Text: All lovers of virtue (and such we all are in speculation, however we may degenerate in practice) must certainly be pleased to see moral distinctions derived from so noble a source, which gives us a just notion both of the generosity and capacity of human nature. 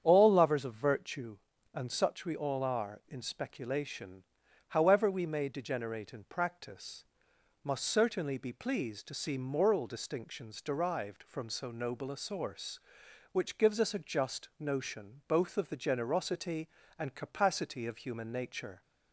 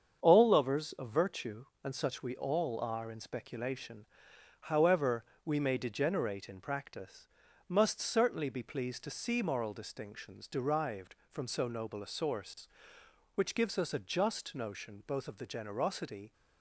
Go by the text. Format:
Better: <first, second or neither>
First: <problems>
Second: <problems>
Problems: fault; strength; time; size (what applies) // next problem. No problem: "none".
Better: first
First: starts louder than the rest; strong; until 1.0 s; 8.5 dB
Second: starts louder than the rest; strong; until 1.2 s; 7.5 dB // pauses between "however" and "we"; slight; at 5.2 s; 0.22 s long // stops before "and capacity of human nature"; at 16.3 s